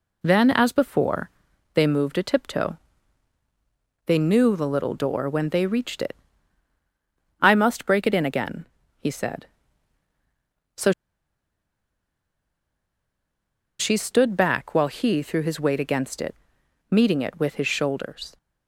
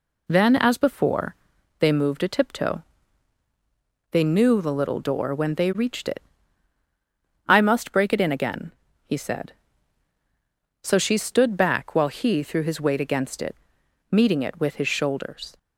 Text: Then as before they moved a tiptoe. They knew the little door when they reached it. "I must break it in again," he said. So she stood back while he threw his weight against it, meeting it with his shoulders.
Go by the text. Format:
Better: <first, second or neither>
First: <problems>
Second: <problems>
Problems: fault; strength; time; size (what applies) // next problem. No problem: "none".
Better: second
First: pauses between "before" and "they"; at 1.3 s; 0.42 s long // pauses between "So" and "she"; strong; at 10.9 s; 2.8 s long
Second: pauses between "before" and "they"; at 1.3 s; 0.42 s long